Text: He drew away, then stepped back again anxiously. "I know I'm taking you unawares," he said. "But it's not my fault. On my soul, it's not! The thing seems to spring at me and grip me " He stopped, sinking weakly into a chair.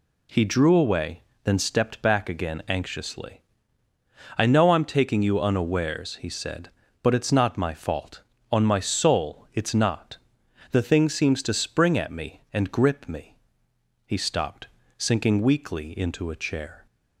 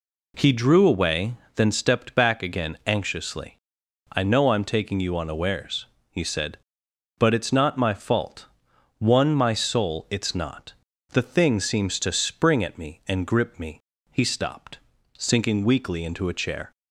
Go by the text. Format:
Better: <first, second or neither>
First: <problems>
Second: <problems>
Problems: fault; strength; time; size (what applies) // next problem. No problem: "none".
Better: first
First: none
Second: says "One" for "On"; at 8.9 s